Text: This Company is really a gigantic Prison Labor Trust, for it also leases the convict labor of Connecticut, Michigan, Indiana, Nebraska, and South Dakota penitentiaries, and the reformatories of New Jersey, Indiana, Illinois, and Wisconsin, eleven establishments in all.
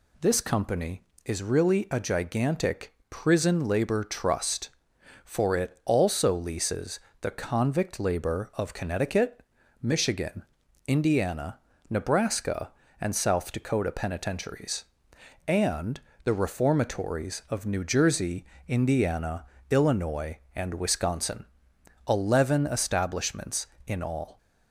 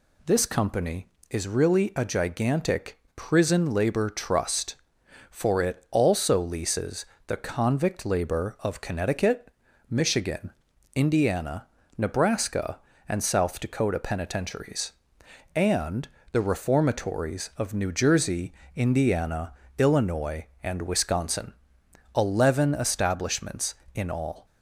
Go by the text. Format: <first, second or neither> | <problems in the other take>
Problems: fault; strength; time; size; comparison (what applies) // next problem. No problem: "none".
neither | pauses between "gigantic" and "Prison"; slight; the same in both // pauses between "leases" and "the"; slight; the same in both // pauses between "and" and "the"; slight; the same in both